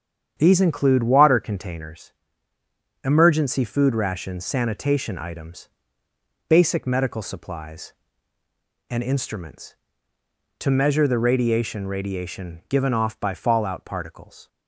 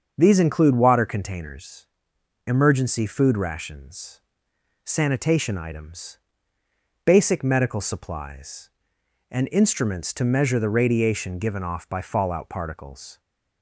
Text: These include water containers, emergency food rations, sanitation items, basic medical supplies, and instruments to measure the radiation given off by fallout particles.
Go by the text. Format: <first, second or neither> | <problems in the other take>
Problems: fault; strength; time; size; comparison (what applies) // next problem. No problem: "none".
second | starts louder than the rest; strong; until 1.3 s; 8 dB; also in the second // says "radiation" twice; at 11.8 s